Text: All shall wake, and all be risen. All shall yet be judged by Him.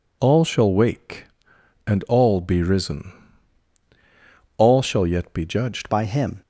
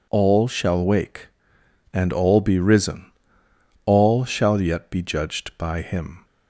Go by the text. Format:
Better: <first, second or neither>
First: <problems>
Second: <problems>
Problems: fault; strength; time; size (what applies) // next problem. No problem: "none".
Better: second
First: changes voice at "by"; from 5.8 s on; 0.6 s long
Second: none